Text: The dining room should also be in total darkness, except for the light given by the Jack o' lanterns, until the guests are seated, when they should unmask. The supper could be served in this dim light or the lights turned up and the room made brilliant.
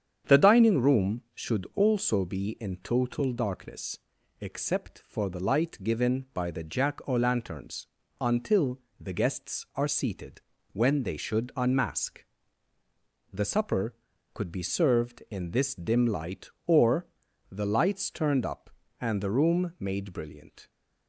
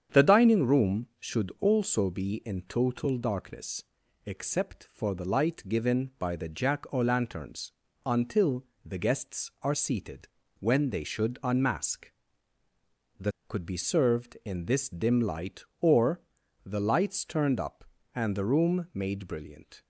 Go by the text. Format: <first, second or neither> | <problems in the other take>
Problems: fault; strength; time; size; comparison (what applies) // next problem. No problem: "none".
first | starts louder than the rest; strong; until 1.2 s; 8 dB; strong in the first // pauses between "until" and "the"; slight; at 8.6 s; 0.20 s long; slight in the first // skips "supper"; at 13.3 s // pauses between "or" and "the"; noticeable; at 16.2 s; 0.46 s long; noticeable in the first